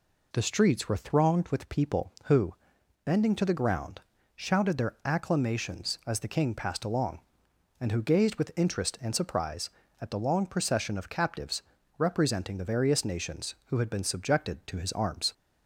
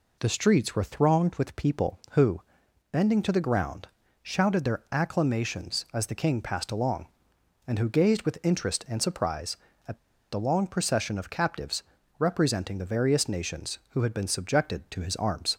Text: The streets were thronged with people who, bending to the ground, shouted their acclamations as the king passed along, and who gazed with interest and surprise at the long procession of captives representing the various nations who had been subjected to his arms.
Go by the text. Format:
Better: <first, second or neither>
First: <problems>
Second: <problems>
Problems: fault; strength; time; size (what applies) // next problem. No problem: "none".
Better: first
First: pauses between "captives" and "representing"; slight; at 11.6 s; 0.36 s long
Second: pauses between "at" and "the"; at 9.9 s; 0.36 s long // pauses between "captives" and "representing"; slight; at 11.8 s; 0.36 s long